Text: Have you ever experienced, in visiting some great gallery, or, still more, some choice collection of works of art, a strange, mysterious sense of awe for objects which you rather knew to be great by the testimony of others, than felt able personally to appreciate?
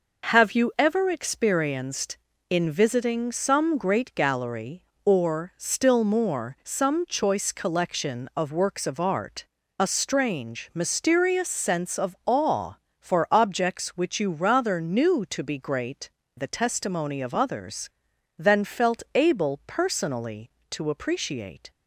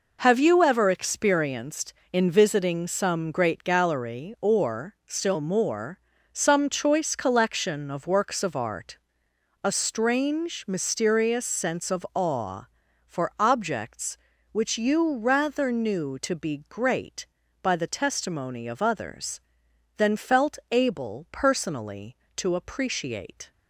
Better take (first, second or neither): second